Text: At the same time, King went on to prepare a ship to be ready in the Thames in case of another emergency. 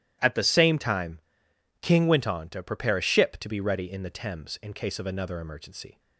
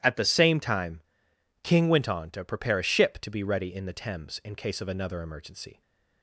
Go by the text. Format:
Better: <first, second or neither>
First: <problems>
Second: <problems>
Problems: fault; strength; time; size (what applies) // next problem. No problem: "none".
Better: neither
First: starts louder than the rest; strong; until 1.8 s; 13 dB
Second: starts louder than the rest; strong; until 1.6 s; 13 dB